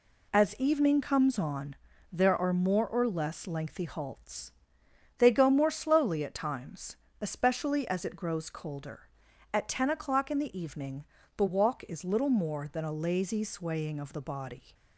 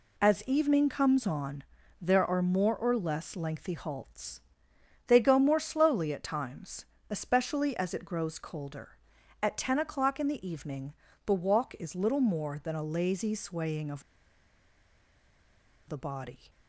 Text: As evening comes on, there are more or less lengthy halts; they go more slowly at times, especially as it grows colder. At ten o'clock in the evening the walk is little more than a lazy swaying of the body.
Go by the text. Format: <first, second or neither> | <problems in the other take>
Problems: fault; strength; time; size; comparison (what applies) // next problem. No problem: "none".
first | pauses between "evening" and "the"; slight; at 10.9 s; 0.32 s long; slight in the first // pauses between "of" and "the"; strong; at 14.0 s; 1.8 s long